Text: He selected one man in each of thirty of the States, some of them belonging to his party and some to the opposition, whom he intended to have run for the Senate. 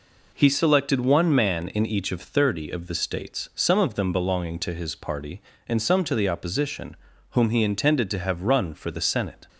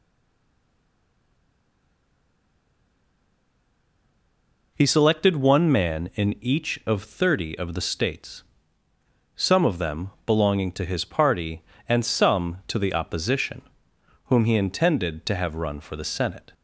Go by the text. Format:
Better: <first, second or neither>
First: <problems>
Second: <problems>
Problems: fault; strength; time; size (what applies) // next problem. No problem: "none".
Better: first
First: none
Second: stays silent before the first word; strong; until 4.7 s; 4.7 s long